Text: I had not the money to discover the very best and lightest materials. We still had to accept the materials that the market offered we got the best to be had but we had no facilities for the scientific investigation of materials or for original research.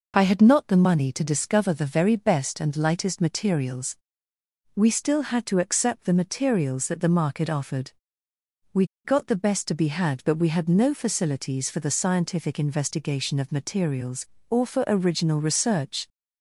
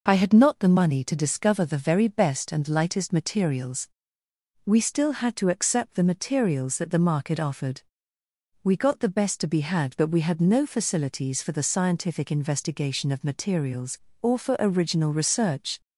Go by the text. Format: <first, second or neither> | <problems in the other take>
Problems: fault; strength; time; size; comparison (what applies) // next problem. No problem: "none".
second | pauses between "offered" and "we"; noticeable; at 7.9 s; 0.82 s long; noticeable in the second // pauses between "we" and "got"; slight; at 8.8 s; 0.19 s long